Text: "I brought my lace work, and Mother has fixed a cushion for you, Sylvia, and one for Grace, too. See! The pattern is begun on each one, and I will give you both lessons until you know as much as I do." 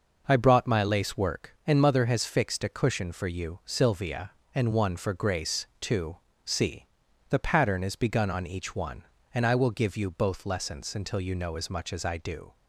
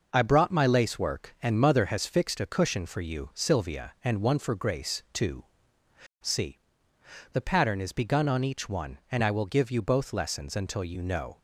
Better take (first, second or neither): first